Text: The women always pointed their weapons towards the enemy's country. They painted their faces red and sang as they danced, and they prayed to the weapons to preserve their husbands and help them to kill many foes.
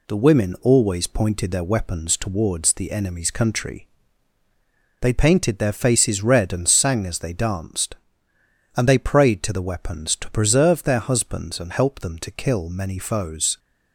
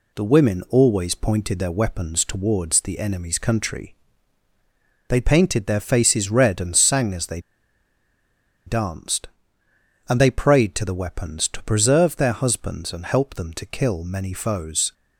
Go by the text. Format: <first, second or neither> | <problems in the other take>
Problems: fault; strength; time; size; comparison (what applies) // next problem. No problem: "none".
first | pauses between "they" and "danced"; strong; at 7.4 s; 1.2 s long